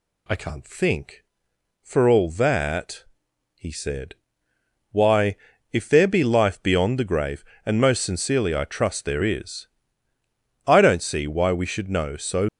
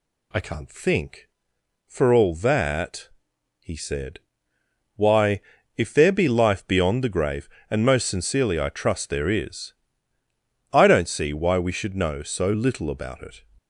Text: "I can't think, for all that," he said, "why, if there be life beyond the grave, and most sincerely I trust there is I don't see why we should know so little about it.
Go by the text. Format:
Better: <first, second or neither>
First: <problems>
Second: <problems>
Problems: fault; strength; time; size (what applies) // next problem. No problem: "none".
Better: second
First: pauses between "is" and "I"; at 9.6 s; 1.0 s long // stops before "little about it"; at 12.4 s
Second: pauses between "is" and "I"; at 9.7 s; 1.0 s long